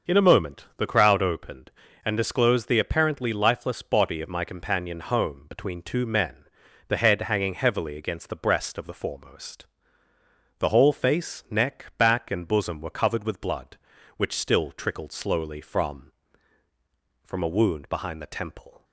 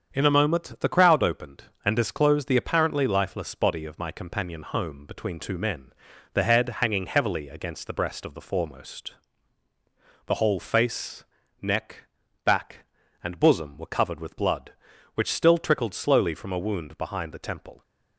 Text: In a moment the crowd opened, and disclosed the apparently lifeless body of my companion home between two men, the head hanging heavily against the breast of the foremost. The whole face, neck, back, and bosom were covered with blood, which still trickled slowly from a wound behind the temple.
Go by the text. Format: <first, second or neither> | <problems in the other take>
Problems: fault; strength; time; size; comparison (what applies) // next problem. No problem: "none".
second | starts louder than the rest; until 1.2 s; 6.5 dB; strong in the second // says "from" twice; at 17.2 s